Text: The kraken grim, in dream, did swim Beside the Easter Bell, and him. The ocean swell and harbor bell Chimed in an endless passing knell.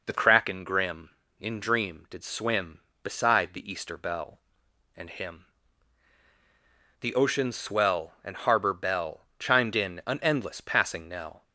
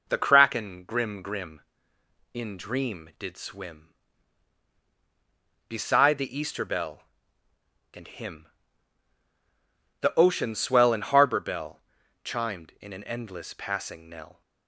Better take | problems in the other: first | says "grim" twice; at 1.2 s // pauses between "bell" and "Chimed"; at 11.7 s; 0.44 s long

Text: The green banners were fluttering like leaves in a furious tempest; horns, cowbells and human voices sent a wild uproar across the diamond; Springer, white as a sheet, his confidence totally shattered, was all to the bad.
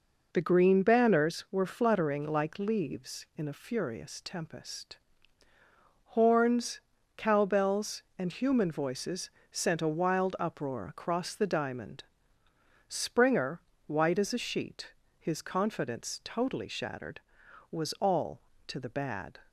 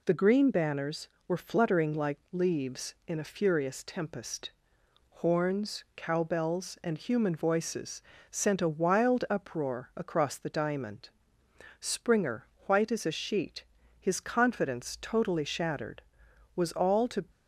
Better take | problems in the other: first | pauses between "voices" and "sent"; slight; at 8.0 s; 0.28 s long; slight in the first // stops before "the bad"; at 17.2 s

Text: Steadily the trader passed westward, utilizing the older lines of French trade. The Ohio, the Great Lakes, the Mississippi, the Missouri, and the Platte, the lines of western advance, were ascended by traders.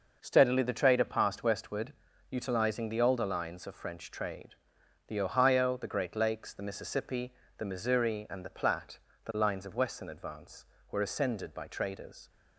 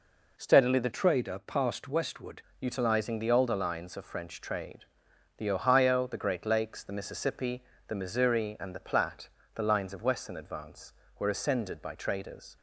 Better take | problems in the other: first | changes voice from "trader" to "westward"; from 0.9 to 2.4 s; 1.5 s long

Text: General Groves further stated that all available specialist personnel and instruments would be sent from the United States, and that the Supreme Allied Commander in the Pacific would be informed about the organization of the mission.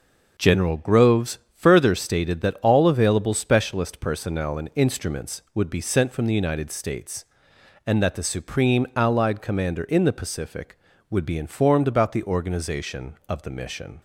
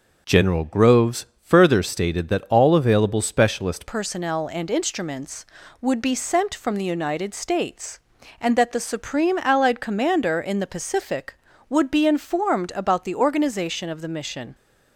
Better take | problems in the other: first | pauses between "Groves" and "further"; slight; at 1.2 s; 0.16 s long; slight in the first // changes voice at "personnel"; from 3.8 s on; 10.7 s long

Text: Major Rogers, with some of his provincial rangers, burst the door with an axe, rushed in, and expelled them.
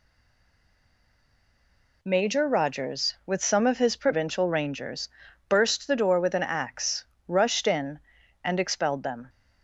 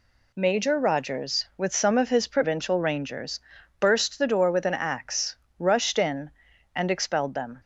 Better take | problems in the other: second | stays silent before the first word; noticeable; until 2.0 s; 2.0 s long

